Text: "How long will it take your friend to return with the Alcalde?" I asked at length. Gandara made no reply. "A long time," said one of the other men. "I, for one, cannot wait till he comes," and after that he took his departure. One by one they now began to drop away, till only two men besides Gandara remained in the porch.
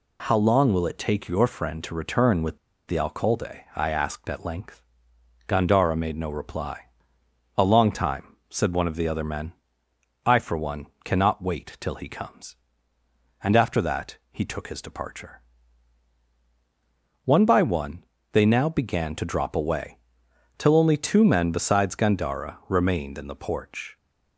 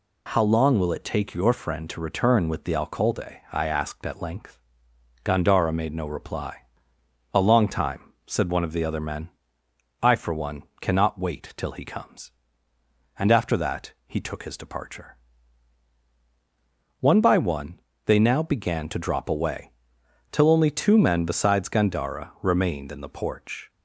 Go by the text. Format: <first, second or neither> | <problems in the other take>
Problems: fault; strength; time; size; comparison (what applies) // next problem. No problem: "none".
second | pauses between "with" and "the"; slight; at 2.5 s; 0.30 s long // pauses between "that" and "he"; slight; at 14.1 s; 0.16 s long; slight in the second // pauses between "one" and "they"; slight; at 18.0 s; 0.30 s long; slight in the second